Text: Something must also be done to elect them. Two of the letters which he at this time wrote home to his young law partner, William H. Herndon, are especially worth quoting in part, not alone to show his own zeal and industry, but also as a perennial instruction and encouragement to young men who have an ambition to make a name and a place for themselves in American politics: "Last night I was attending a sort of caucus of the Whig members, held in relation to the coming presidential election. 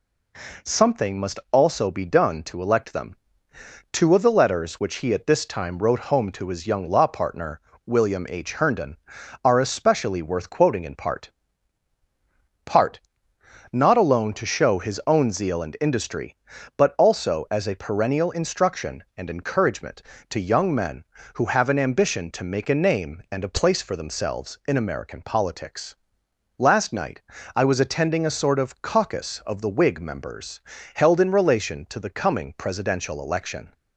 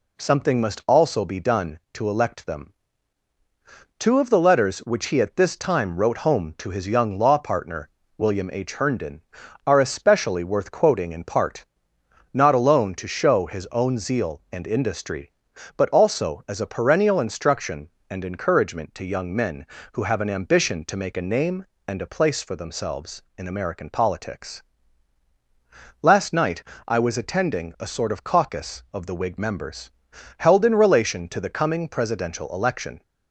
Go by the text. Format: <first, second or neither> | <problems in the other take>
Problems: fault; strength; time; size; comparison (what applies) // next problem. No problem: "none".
second | says "part" twice; at 12.6 s // pauses between "night" and "I"; slight; at 27.1 s; 0.36 s long; slight in the second